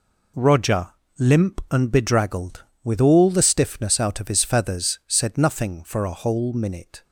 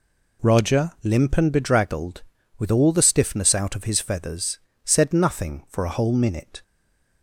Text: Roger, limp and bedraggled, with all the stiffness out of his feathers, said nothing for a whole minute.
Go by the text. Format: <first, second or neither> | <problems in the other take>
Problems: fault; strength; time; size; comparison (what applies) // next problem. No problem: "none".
first | stays silent after the last word; slight; from 6.6 s on; 0.6 s long